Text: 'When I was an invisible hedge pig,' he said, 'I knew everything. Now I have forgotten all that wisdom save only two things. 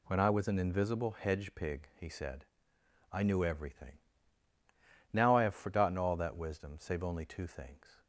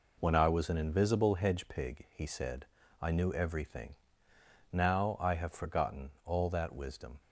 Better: first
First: none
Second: stops before "save only two things"; at 7.2 s

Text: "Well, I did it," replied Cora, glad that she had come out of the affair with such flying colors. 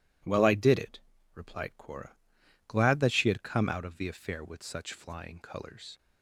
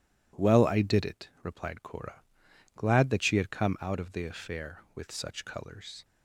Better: first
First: none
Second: skips "flying"; at 5.4 s

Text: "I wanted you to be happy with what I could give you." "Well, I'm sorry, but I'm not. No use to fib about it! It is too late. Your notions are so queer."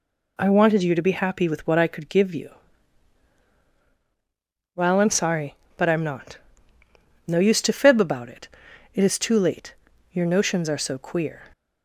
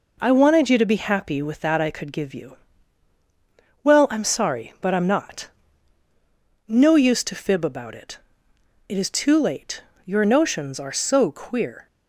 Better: first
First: none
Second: says "that" for "what"; at 1.6 s

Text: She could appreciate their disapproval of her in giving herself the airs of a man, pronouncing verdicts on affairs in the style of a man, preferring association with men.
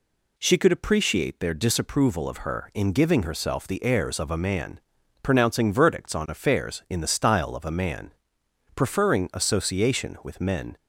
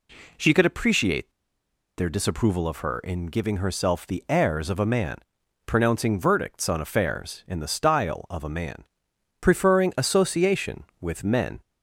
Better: first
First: none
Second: pauses between "appreciate" and "their"; noticeable; at 1.3 s; 0.66 s long

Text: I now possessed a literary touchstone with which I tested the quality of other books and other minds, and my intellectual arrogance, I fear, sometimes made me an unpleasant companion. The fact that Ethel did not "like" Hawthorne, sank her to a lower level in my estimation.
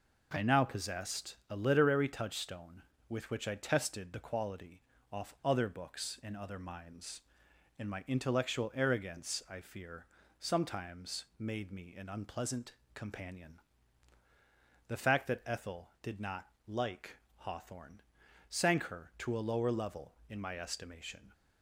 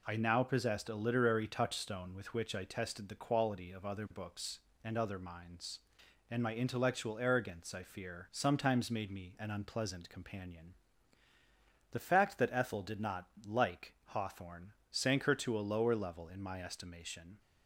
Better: second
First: says "off" for "of"; at 5.1 s // pauses between "unpleasant" and "companion"; slight; at 12.7 s; 0.22 s long // pauses between "not" and "like"; slight; at 16.4 s; 0.20 s long // pauses between "like" and "Hawthorne"; slight; at 17.1 s; 0.18 s long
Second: none

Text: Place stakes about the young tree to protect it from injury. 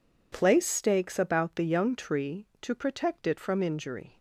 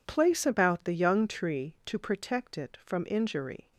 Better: first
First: none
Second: skips "stakes"; at 0.4 s

